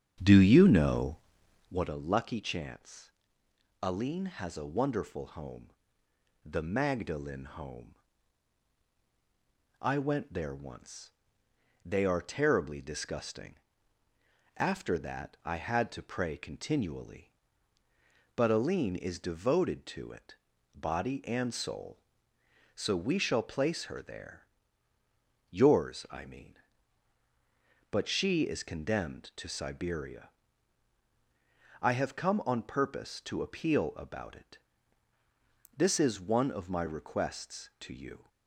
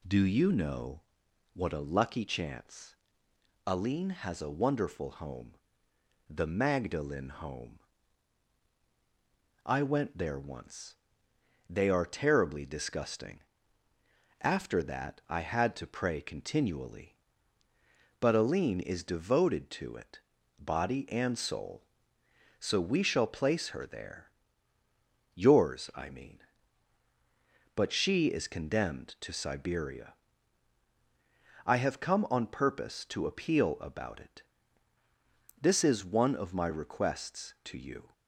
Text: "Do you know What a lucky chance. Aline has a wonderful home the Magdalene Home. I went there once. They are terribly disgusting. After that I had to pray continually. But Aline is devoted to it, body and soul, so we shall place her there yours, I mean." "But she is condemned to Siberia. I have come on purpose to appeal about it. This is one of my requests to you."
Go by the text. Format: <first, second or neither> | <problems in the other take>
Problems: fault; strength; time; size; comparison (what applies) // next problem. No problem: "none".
second | starts louder than the rest; strong; until 1.9 s; 8 dB // pauses between "know" and "What"; noticeable; at 1.1 s; 0.54 s long; noticeable in the second // pauses between "home" and "the"; noticeable; at 5.6 s; 0.74 s long; noticeable in the second // pauses between "there" and "yours"; at 24.4 s; 1.0 s long; also in the second